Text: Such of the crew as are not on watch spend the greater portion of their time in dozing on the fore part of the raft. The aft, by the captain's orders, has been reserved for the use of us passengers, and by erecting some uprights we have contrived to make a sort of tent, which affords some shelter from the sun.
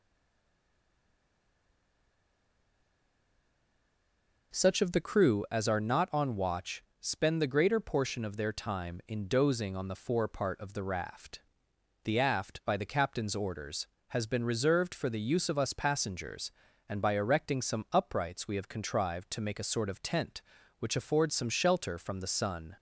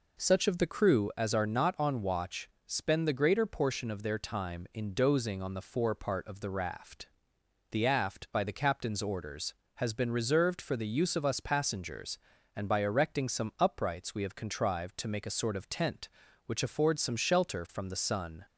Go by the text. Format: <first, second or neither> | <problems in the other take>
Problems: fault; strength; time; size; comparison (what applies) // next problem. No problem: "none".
second | stays silent before the first word; strong; until 4.5 s; 4.5 s long // pauses between "watch" and "spend"; slight; at 6.8 s; 0.16 s long; slight in the second